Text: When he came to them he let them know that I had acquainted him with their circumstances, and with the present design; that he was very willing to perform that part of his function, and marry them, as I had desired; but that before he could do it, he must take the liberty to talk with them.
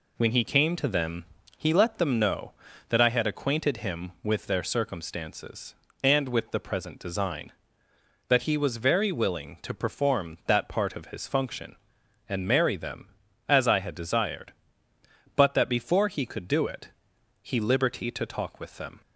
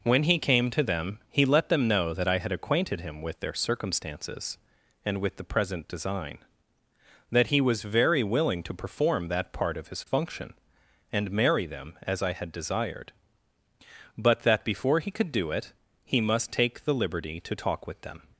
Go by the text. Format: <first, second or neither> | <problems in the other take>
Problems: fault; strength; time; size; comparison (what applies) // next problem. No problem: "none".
second | pauses between "them" and "he"; slight; at 1.2 s; 0.34 s long // skips "must take the"; at 17.5 s